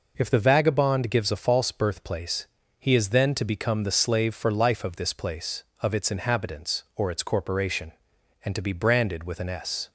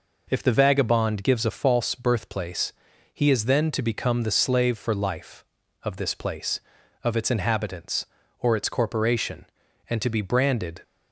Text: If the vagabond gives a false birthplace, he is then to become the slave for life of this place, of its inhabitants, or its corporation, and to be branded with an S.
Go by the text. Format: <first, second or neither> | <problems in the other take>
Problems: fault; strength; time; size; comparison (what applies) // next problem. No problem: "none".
first | stops before "with an S"; at 10.8 s